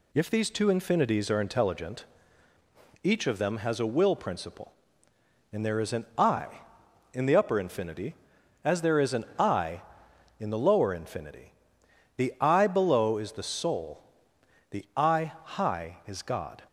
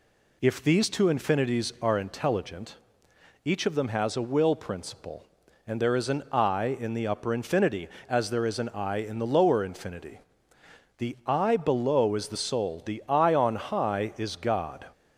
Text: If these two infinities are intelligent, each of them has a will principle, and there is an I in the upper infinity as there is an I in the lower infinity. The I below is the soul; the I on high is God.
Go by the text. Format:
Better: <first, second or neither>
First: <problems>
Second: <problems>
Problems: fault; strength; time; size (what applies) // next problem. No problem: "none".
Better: second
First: skips "on"; at 15.3 s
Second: none